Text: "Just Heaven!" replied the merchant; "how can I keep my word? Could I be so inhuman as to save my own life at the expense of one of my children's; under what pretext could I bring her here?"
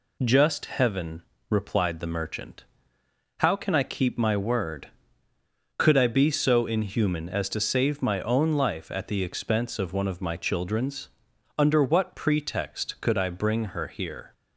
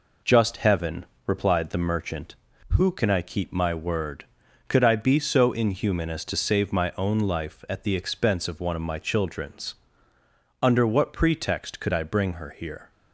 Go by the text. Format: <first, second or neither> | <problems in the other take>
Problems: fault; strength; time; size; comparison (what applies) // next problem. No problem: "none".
first | says "who" for "how"; at 2.6 s